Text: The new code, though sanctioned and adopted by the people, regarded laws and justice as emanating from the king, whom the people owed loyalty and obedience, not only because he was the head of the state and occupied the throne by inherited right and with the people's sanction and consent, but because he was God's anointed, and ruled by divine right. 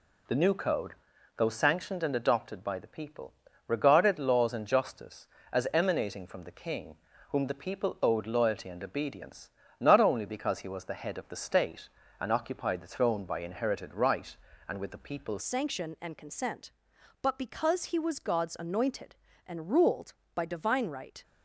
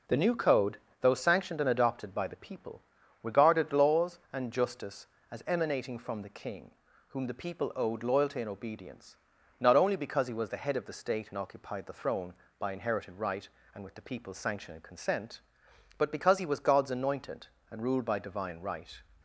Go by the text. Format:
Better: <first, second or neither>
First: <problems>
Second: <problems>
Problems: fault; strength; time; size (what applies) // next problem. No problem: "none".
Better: second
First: changes voice at "sanction"; from 15.4 s on; 5.8 s long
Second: none